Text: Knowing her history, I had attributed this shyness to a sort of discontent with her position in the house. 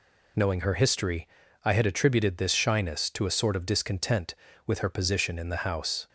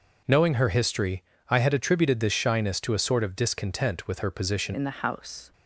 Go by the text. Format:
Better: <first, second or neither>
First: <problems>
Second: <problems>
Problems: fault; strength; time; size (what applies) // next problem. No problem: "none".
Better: first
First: none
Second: changes voice at "in"; from 4.7 s on; 0.8 s long